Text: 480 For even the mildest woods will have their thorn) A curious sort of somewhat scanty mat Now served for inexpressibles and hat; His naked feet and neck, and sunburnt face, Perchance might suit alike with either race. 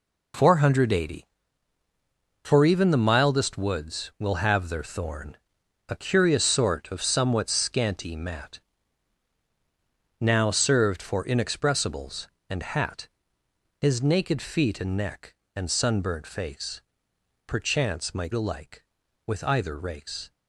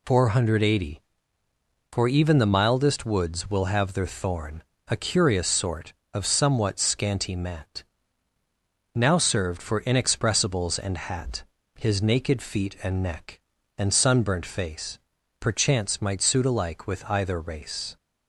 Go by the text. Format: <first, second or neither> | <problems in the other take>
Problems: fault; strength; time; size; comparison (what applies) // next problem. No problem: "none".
second | pauses between "mat" and "Now"; strong; at 8.5 s; 1.6 s long; also in the second // skips "suit"; at 18.3 s